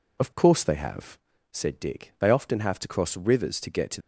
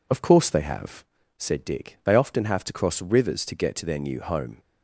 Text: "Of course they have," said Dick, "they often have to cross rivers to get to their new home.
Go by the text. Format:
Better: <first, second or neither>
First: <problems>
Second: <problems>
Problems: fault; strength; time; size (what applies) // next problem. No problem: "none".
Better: second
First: stops before "their new home"; at 4.0 s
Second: none